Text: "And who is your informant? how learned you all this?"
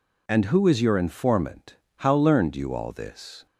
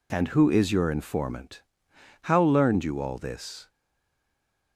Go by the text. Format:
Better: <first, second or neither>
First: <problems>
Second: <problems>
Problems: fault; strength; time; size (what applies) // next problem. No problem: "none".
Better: first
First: none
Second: stays silent after the last word; from 3.6 s on; 1.1 s long